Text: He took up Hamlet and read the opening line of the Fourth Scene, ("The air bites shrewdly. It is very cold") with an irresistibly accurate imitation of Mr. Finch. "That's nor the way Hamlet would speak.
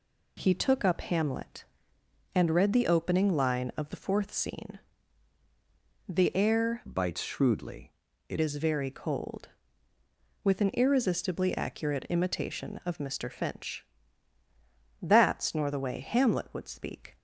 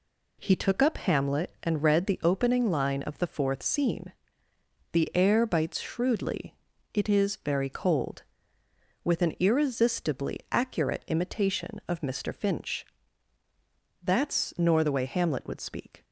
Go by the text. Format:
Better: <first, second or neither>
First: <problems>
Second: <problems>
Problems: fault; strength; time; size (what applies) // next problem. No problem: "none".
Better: second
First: changes voice from "bites" to "It"; from 6.8 to 8.3 s; 1.5 s long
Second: none